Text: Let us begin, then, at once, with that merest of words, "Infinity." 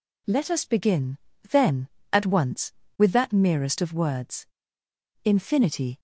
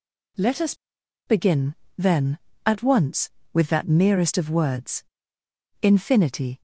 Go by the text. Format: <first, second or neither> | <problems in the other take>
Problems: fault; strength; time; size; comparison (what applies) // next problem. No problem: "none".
first | pauses between "us" and "begin"; noticeable; at 0.7 s; 0.52 s long